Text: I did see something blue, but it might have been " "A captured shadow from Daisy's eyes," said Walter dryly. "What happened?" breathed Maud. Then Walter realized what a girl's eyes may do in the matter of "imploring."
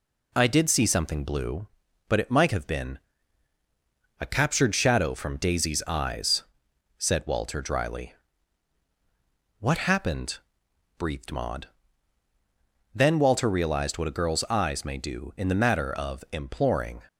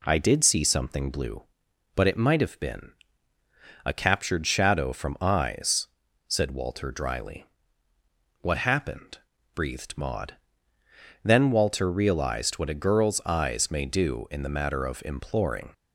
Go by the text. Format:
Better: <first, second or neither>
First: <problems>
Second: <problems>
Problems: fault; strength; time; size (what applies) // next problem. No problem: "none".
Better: first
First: none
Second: skips "Daisy's"; at 5.1 s